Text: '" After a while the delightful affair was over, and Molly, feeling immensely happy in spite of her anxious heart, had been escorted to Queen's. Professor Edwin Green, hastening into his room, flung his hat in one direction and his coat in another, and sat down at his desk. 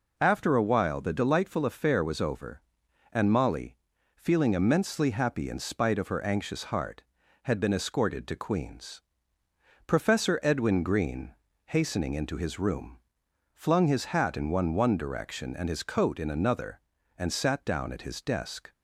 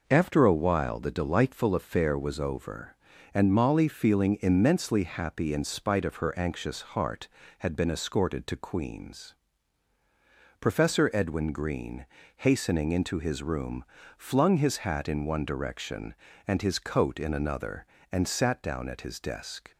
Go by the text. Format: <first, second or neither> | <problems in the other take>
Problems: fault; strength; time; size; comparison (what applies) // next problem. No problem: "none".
second | says "one" twice; at 14.7 s